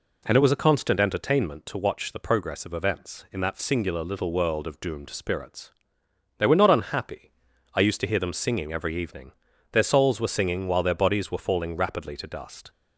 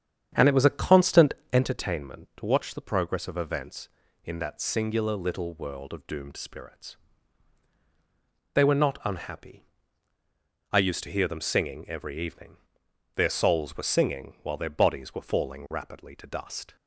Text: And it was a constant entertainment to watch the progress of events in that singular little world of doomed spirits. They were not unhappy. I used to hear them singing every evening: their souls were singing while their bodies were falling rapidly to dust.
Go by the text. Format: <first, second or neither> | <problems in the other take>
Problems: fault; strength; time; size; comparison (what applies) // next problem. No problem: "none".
first | starts louder than the rest; strong; until 1.7 s; 8.5 dB // pauses between "constant" and "entertainment"; slight; at 1.3 s; 0.18 s long